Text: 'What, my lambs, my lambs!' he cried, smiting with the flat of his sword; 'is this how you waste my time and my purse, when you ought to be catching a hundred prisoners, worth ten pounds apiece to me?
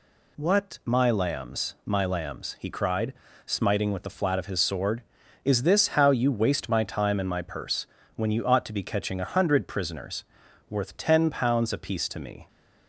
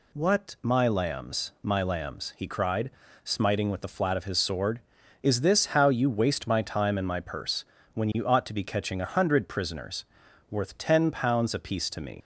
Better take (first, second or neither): first